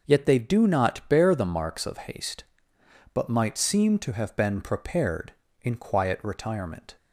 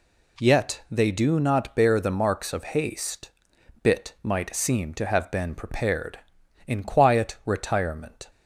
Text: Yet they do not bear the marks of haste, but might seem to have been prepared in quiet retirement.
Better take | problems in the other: first | says "bit" for "but"; at 3.8 s

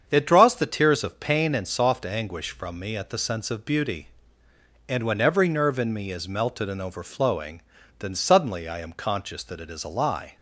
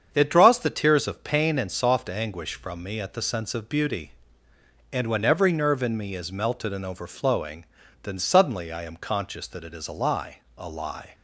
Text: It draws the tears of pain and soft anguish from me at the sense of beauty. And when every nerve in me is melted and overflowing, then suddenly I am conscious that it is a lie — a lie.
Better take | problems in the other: second | starts louder than the rest; strong; until 1.0 s; 7.5 dB; strong in the second // stops before "a lie"; at 10.3 s

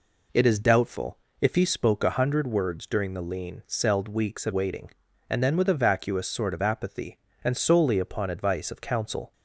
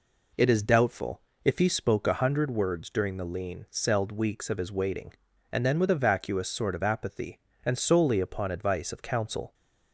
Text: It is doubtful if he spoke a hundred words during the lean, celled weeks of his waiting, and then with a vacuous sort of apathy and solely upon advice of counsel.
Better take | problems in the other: second | pauses between "doubtful" and "if"; slight; at 1.1 s; 0.24 s long; slight in the second // skips "his"; at 4.5 s

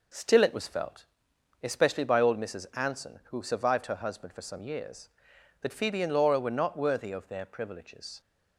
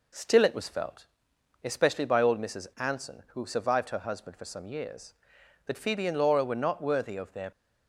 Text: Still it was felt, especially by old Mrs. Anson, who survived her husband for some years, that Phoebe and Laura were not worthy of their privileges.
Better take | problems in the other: first | stops before "privileges"; at 7.5 s

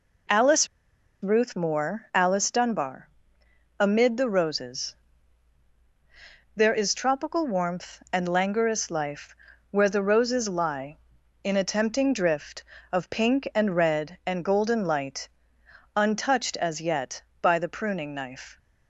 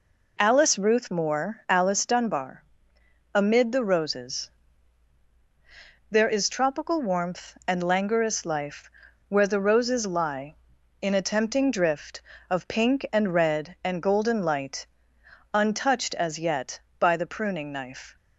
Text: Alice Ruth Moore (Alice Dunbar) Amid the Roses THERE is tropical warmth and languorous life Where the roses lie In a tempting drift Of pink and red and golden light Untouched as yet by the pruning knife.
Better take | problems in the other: second | pauses between "Alice" and "Ruth"; noticeable; at 0.6 s; 0.55 s long // pauses between "Roses" and "THERE"; strong; at 4.9 s; 1.6 s long; strong in the second // pauses between "life" and "Where"; slight; at 9.3 s; 0.34 s long; also in the second // pauses between "light" and "Untouched"; noticeable; at 15.2 s; 0.68 s long; noticeable in the second

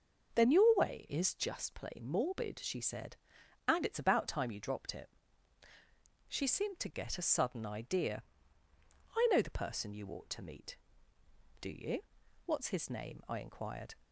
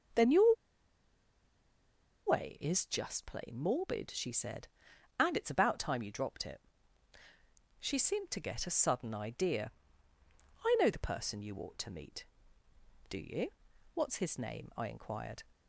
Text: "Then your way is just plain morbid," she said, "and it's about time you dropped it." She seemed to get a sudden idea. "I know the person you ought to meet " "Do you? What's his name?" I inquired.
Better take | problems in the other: first | pauses between "your" and "way"; strong; at 0.5 s; 1.7 s long

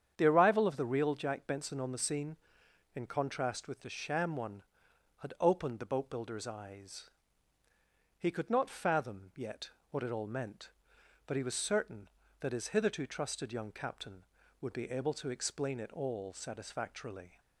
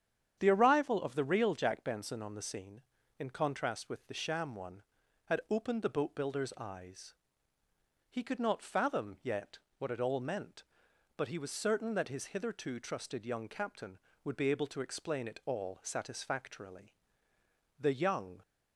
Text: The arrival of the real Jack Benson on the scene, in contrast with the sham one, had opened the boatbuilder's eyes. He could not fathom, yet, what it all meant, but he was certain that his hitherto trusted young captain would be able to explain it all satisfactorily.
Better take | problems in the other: first | starts louder than the rest; strong; until 1.4 s; 8.5 dB; strong in the first // goes on to say "The young"; noticeable; from 17.7 s on; 0.62 s long

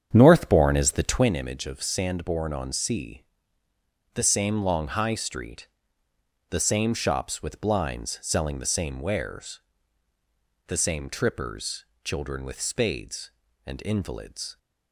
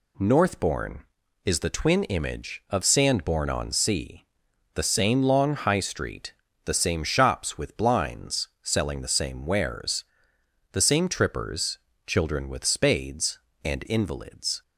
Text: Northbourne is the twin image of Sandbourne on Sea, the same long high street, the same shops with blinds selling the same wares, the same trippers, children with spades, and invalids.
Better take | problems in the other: second | starts louder than the rest; strong; until 1.2 s; 8.5 dB

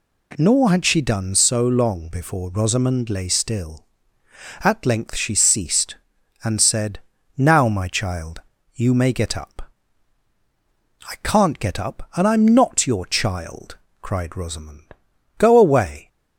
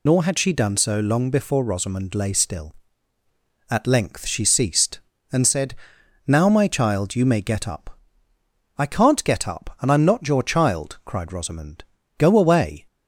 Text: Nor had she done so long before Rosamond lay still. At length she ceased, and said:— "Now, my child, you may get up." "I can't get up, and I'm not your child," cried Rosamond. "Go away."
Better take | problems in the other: first | loses the start of "Nor"; at 0.0 s; 35 ms

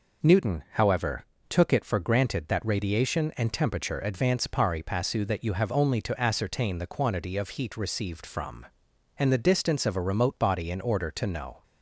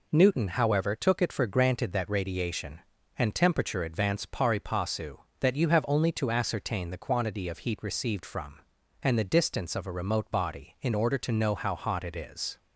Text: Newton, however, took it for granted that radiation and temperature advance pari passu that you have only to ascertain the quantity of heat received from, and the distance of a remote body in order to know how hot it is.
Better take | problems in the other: second | stops before "how hot it is"; at 11.6 s

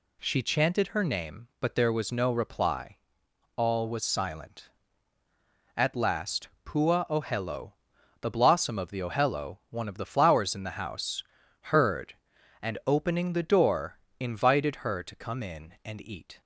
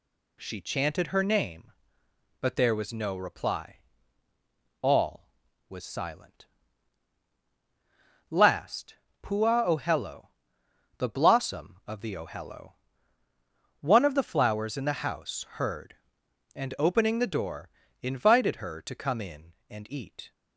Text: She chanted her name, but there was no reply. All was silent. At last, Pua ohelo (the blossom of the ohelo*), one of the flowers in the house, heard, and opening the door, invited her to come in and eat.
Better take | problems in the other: first | skips "At"; at 7.3 s

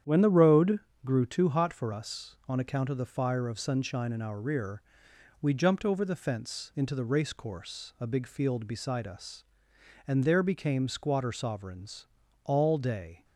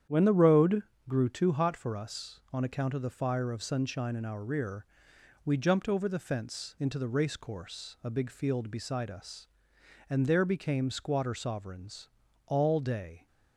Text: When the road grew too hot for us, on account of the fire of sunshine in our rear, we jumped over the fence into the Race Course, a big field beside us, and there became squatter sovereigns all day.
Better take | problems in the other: neither | starts louder than the rest; strong; the same in both // pauses between "road" and "grew"; slight; the same in both // pauses between "sovereigns" and "all"; the same in both

